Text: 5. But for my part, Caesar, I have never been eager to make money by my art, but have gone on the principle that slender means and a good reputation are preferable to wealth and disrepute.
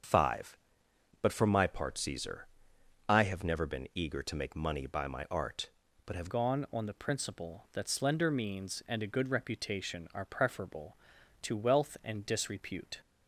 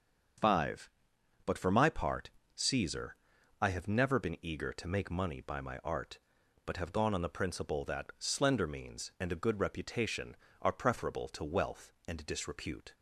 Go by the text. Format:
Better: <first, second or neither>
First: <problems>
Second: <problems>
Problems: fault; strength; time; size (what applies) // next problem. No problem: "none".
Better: second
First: starts louder than the rest; strong; until 1.7 s; 7 dB // changes voice at "gone"; from 6.2 s on; 6.8 s long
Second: starts louder than the rest; until 1.9 s; 7 dB